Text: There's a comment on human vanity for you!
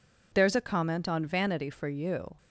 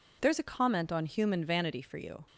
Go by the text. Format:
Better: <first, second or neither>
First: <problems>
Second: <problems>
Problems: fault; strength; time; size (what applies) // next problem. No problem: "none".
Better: second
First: skips "human"; at 1.2 s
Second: none